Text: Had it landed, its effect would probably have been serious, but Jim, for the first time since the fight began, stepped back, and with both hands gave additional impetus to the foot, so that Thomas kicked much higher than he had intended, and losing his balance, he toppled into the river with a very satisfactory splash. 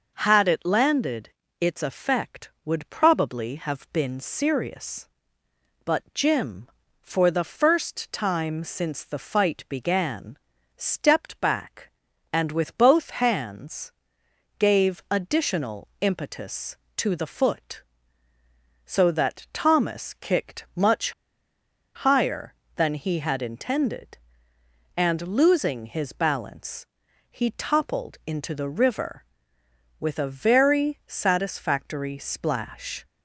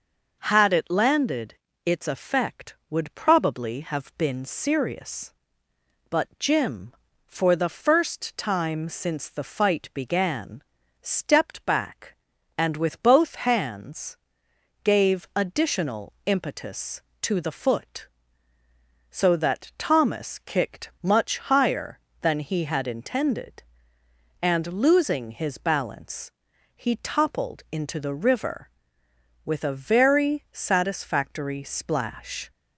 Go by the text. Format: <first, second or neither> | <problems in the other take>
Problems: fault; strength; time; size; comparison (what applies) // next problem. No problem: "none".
second | pauses between "hands" and "gave"; noticeable; at 13.9 s; 0.68 s long; noticeable in the second // pauses between "much" and "higher"; noticeable; at 21.1 s; 0.83 s long